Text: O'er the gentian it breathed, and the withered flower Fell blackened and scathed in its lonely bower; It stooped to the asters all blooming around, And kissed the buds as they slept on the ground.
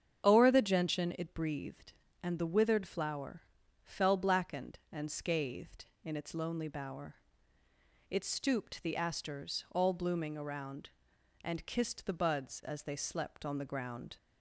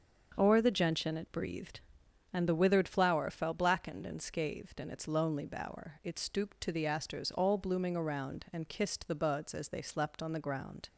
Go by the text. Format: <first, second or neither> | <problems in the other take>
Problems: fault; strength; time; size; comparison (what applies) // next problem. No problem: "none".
second | starts louder than the rest; strong; until 1.2 s; 8 dB; also in the second // pauses between "flower" and "Fell"; at 3.4 s; 0.42 s long // skips "to"; at 8.8 s